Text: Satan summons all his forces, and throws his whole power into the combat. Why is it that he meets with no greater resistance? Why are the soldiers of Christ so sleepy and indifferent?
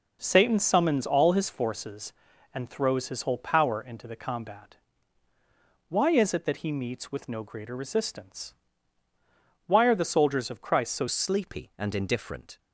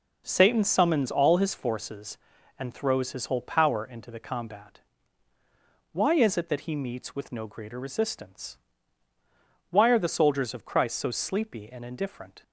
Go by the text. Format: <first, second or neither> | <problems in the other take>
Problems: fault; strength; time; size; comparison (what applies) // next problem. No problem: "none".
second | changes voice at "sleepy"; from 11.0 s on; 1.5 s long